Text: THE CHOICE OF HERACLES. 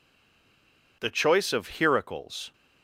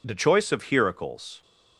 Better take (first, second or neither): second